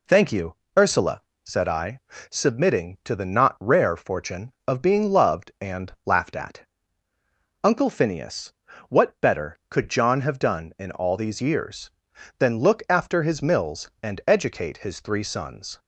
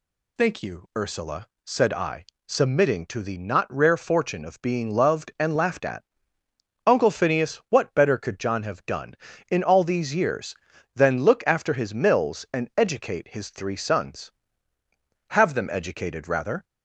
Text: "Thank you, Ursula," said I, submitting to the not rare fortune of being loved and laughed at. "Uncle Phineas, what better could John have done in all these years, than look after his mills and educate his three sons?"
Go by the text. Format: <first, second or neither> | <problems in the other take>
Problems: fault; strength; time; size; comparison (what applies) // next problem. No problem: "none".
first | goes on to say "Have them educated rather"; from 15.3 s on; 1.3 s long